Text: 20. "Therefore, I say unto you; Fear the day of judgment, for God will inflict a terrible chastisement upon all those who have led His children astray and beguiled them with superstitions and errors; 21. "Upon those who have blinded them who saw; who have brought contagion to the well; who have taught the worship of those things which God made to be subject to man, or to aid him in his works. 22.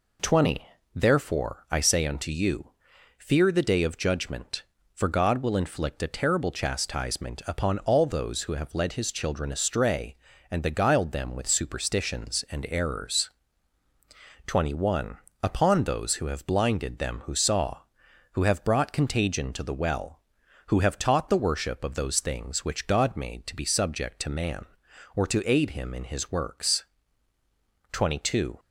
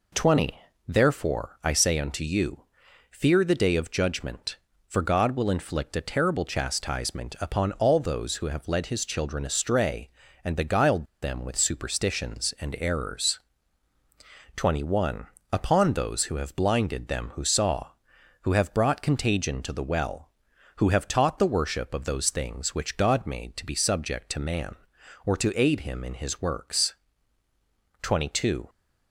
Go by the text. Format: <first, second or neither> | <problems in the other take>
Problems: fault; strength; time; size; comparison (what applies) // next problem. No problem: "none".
first | pauses between "beguiled" and "them"; slight; at 11.0 s; 0.16 s long